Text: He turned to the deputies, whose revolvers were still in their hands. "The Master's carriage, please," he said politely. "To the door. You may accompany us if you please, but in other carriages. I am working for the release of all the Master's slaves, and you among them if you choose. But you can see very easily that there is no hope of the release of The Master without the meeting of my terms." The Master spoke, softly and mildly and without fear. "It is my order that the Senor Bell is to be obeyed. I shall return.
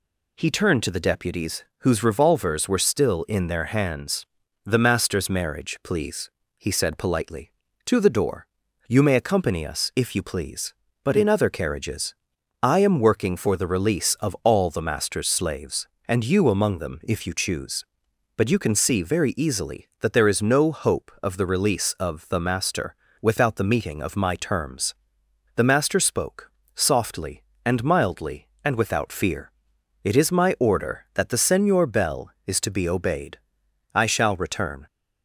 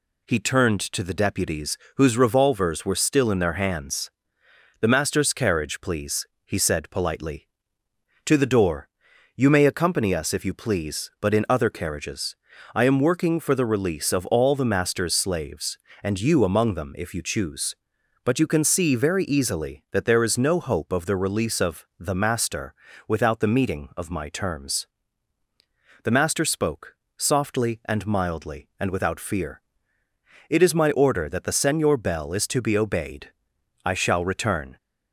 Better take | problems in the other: second | says "marriage" for "carriage"; at 5.2 s // pauses between "Master" and "without"; slight; at 22.9 s; 0.28 s long; slight in the second

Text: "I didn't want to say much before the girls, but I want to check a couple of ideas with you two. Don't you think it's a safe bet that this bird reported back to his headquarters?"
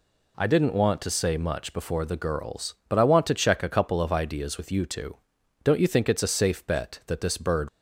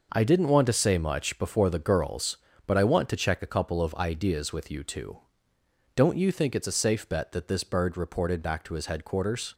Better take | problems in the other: second | stops before "reported back to his headquarters"; at 7.6 s

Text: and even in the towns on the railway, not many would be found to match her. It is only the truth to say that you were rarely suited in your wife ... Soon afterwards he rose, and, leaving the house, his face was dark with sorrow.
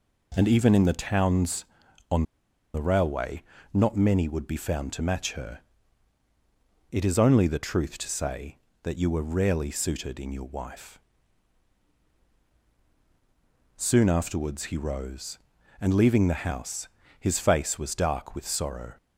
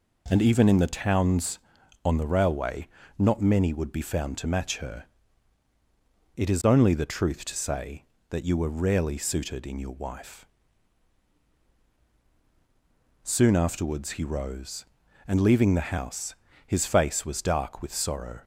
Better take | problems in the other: second | pauses between "on" and "the"; noticeable; at 2.2 s; 0.51 s long

